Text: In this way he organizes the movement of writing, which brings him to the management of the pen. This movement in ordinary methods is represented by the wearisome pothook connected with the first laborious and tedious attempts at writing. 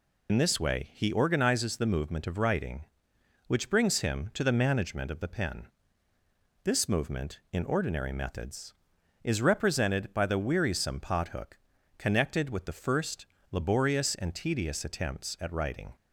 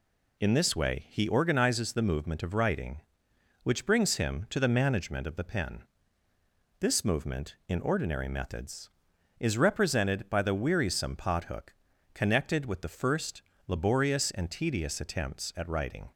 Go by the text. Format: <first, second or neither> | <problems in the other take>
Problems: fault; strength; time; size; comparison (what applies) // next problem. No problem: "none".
second | loses the start of "In"; at 0.2 s; 55 ms // pauses between "pothook" and "connected"; at 11.5 s; 0.42 s long; also in the second // pauses between "first" and "laborious"; slight; at 13.2 s; 0.24 s long; slight in the second